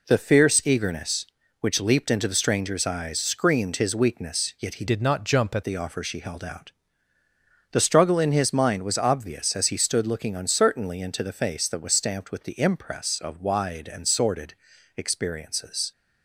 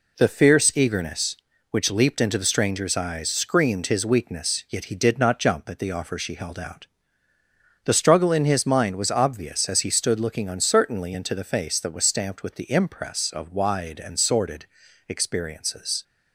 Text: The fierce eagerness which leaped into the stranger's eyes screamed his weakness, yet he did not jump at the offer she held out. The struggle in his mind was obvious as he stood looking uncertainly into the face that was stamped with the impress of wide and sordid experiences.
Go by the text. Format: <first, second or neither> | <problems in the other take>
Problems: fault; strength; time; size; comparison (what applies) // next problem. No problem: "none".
second | changes voice from "did" to "at"; from 4.8 to 5.6 s; 0.8 s long // pauses between "sordid" and "experiences"; at 14.5 s; 0.42 s long; also in the second